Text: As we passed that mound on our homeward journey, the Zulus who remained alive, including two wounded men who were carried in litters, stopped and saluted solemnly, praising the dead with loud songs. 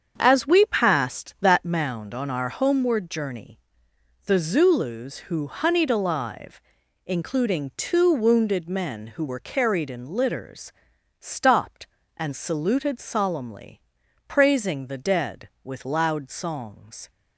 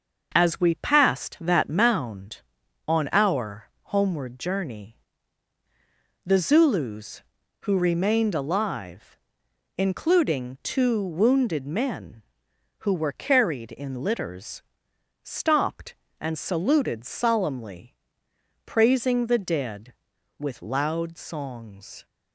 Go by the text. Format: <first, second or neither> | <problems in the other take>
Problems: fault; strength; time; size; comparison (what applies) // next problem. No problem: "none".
second | starts louder than the rest; strong; until 1.2 s; 7.5 dB; noticeable in the second // says "honeyed" for "remained"; at 5.4 s